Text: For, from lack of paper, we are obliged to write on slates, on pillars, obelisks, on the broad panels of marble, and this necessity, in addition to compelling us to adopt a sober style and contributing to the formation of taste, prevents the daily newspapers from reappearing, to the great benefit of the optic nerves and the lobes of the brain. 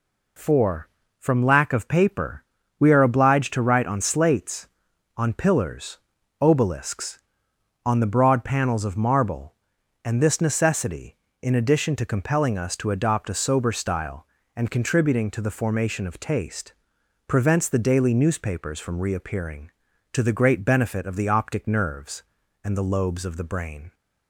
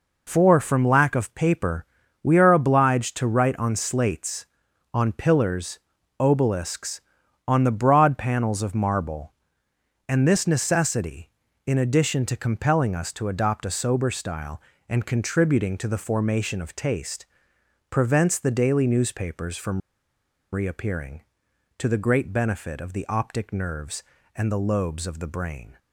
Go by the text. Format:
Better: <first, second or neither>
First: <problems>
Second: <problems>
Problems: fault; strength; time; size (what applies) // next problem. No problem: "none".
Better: first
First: none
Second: pauses between "from" and "reappearing"; noticeable; at 19.8 s; 0.73 s long